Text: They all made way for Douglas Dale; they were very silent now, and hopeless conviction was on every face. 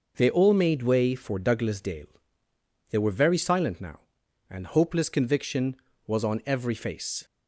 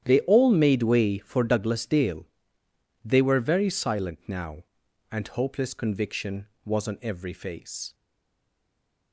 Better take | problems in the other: first | starts louder than the rest; strong; until 1.0 s; 10 dB // stays silent after the last word; noticeable; from 7.9 s on; 1.2 s long

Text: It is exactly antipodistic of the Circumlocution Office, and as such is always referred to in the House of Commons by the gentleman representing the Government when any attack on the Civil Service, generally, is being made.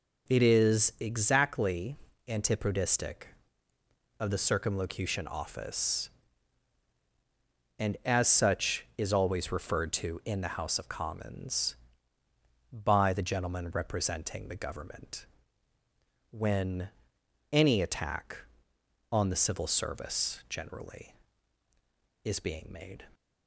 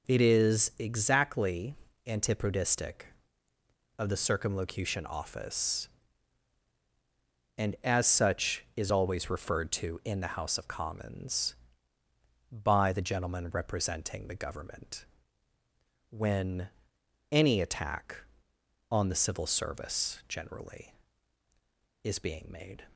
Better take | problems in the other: neither | pauses between "exactly" and "antipodistic"; slight; the same in both // pauses between "Government" and "when"; the same in both // pauses between "when" and "any"; noticeable; the same in both

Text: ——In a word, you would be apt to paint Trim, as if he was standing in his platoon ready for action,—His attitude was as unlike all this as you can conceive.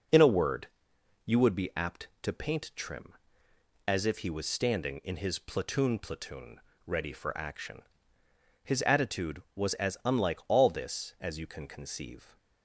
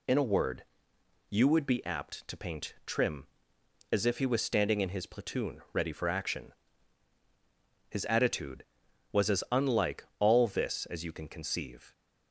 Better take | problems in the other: second | says "platoon" twice; at 5.9 s

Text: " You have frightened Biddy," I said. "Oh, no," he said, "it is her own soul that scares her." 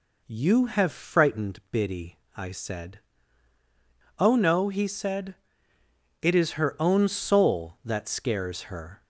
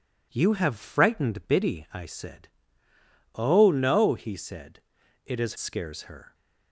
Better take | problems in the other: first | skips "her own soul that"; at 5.5 s

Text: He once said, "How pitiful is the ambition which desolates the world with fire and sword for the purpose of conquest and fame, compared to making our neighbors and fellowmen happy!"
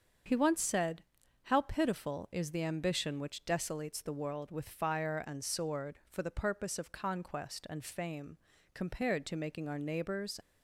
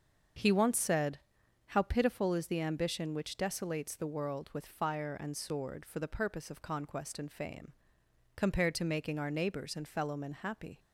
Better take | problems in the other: second | starts louder than the rest; until 1.6 s; 7 dB; also in the second // stops before "and fellowmen happy"; at 10.4 s

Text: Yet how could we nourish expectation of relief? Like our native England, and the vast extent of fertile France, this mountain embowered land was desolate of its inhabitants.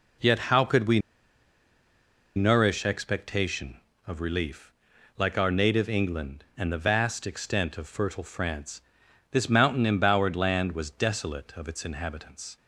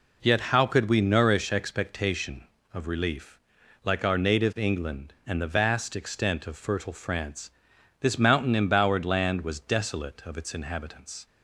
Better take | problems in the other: second | pauses between "we" and "nourish"; strong; at 0.9 s; 1.3 s long

